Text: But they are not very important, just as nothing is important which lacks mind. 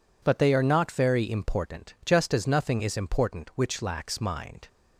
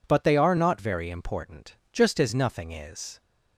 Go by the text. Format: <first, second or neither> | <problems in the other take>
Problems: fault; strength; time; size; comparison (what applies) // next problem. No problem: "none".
first | stops before "important which lacks mind"; at 3.2 s